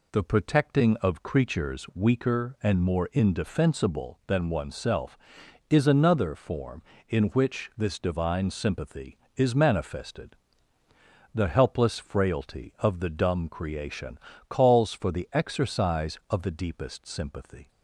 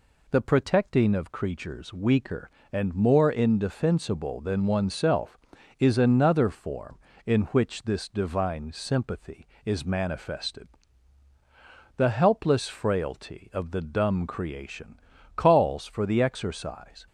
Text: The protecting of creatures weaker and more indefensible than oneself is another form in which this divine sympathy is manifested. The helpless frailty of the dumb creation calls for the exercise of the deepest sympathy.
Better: first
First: pauses between "creation" and "calls"; slight; at 14.1 s; 0.30 s long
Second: pauses between "creation" and "calls"; at 14.9 s; 0.38 s long // stops before "of the deepest sympathy"; at 17.0 s

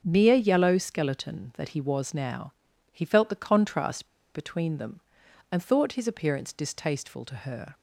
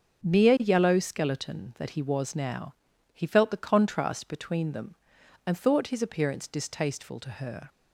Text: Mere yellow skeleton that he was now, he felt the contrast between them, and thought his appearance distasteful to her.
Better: second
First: starts louder than the rest; until 1.0 s; 6.5 dB // pauses between "contrast" and "between"; slight; at 4.0 s; 0.29 s long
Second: starts louder than the rest; until 1.3 s; 6.5 dB

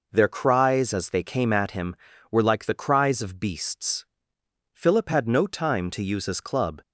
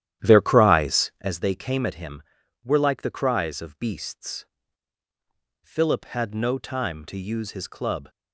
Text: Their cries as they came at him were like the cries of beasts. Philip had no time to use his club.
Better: first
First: none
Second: starts louder than the rest; strong; until 1.4 s; 11.5 dB

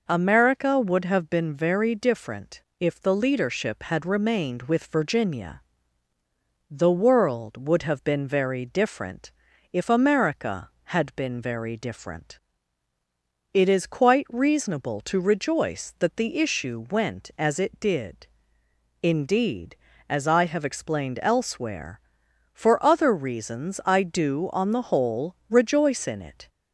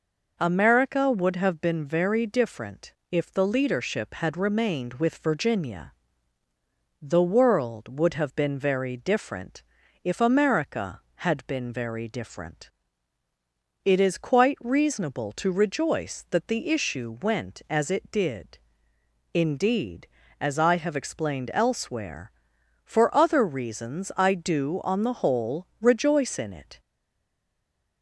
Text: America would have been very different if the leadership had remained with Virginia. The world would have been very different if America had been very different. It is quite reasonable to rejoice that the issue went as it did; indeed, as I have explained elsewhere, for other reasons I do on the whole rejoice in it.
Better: first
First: pauses between "different" and "if"; slight; at 2.5 s; 0.18 s long // pauses between "different" and "if"; at 9.3 s; 0.40 s long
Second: pauses between "different" and "if"; slight; at 2.9 s; 0.18 s long // pauses between "different" and "if"; at 9.6 s; 0.40 s long // stays silent after the last word; noticeable; from 26.8 s on; 1.2 s long

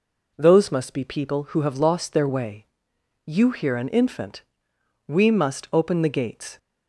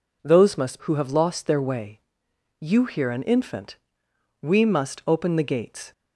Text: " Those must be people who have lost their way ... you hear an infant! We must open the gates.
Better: first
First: none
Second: skips "be people"; at 0.8 s

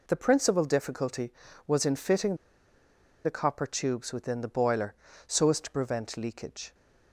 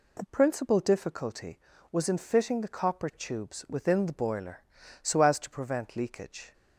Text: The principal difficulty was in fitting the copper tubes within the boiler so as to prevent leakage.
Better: second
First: pauses between "fitting" and "the"; noticeable; at 2.3 s; 0.90 s long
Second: none

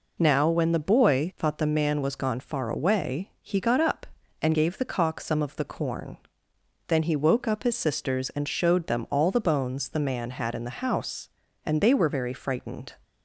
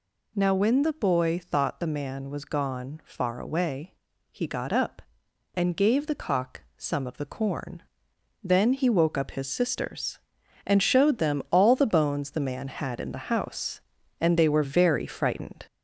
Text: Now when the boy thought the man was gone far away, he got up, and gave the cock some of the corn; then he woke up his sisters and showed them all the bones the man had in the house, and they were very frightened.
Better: first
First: none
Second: gets louder; throughout; 4 dB

